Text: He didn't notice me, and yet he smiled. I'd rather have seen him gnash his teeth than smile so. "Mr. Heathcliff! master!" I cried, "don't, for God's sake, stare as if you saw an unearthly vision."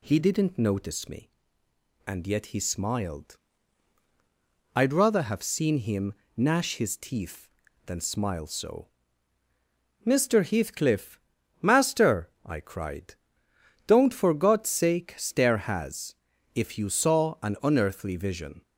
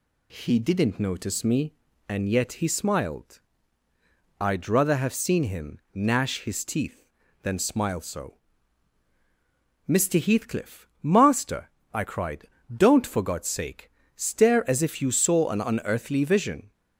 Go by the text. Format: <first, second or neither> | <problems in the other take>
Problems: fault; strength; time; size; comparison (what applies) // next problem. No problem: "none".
second | pauses between "him" and "gnash"; slight; at 6.1 s; 0.20 s long // says "has" for "as"; at 15.5 s